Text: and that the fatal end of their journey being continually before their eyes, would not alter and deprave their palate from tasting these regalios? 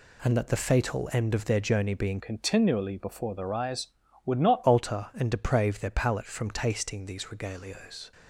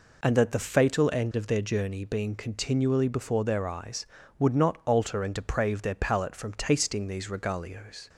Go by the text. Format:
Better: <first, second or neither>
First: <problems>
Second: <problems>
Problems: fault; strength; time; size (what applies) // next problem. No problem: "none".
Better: second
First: changes voice from "continually" to "not"; from 2.1 to 4.6 s; 2.5 s long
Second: none